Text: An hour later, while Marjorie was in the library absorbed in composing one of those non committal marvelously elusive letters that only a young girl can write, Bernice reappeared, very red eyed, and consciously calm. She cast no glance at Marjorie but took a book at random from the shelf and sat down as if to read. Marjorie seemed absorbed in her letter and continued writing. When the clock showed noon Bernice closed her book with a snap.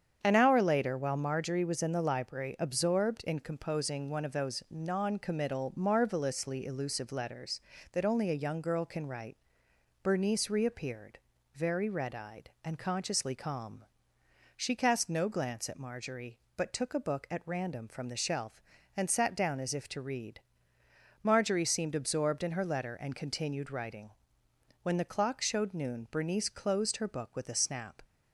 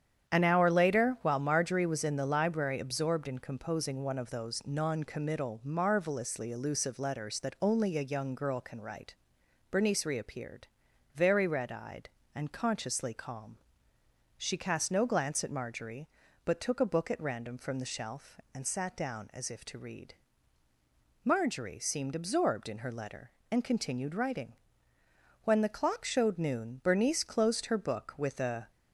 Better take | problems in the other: first | starts louder than the rest; strong; until 1.3 s; 9 dB; strong in the first // stops before "snap"; at 28.6 s

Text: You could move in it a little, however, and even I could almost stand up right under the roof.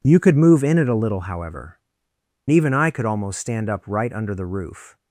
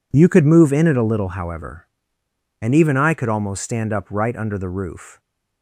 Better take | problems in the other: second | skips "and"; at 2.1 s

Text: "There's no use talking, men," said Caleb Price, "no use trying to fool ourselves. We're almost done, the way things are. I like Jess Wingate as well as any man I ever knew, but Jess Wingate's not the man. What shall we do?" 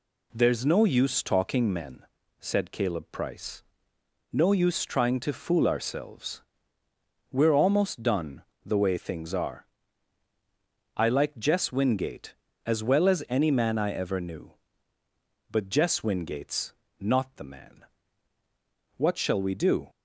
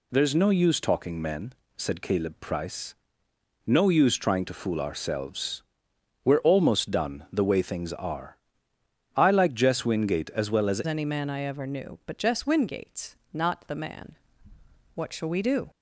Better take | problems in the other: first | changes voice at "any"; from 10.8 s on; 4.9 s long // pauses between "Wingate's" and "not"; slight; at 13.1 s; 0.16 s long; slight in the first

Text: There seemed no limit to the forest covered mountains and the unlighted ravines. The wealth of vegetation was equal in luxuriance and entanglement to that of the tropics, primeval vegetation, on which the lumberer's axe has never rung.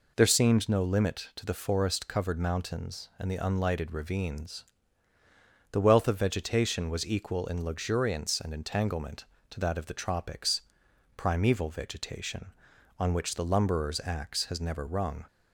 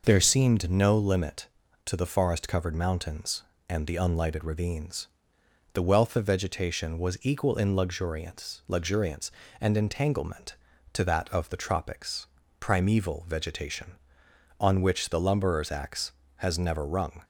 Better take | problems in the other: first | says "luxuriance" twice; at 8.6 s

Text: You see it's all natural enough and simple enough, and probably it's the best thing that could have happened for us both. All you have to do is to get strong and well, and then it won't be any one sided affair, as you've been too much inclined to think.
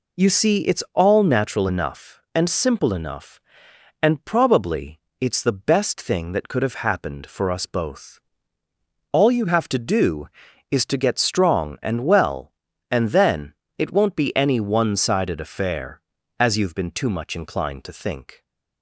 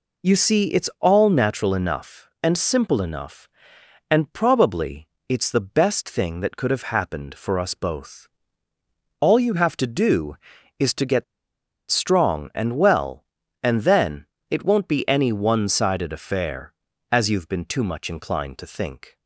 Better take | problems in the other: first | pauses between "probably" and "it's"; slight; at 5.0 s; 0.22 s long; slight in the first // pauses between "get" and "strong"; noticeable; at 11.2 s; 0.66 s long // pauses between "then" and "it"; slight; at 14.2 s; 0.24 s long; slight in the first

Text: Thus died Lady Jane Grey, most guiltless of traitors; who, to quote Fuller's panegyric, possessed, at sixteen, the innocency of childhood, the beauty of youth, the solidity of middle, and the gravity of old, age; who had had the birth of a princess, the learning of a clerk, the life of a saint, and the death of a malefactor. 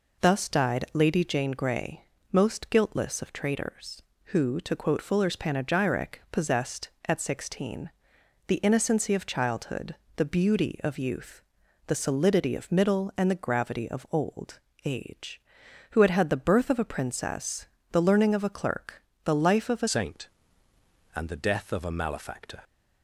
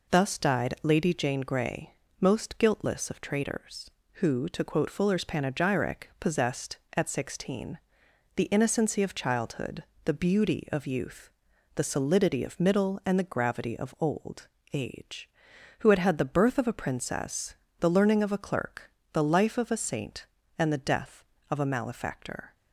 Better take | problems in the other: second | changes voice at "saint"; from 19.8 s on; 2.8 s long

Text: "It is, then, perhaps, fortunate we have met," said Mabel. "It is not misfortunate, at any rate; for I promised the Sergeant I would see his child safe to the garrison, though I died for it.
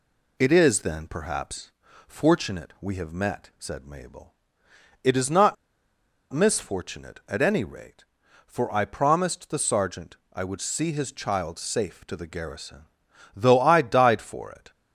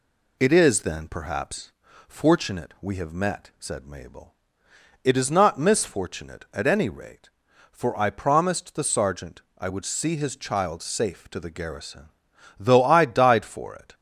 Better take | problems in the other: second | pauses between "not" and "misfortunate"; noticeable; at 5.5 s; 0.77 s long // pauses between "Sergeant" and "I"; slight; at 10.1 s; 0.16 s long; slight in the second

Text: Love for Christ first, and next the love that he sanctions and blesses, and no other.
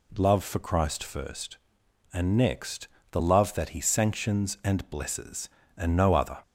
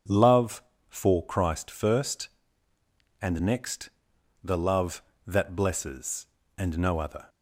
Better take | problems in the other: first | pauses between "next" and "the"; noticeable; at 3.8 s; 0.52 s long; slight in the first // skips "he sanctions and"; at 5.5 s

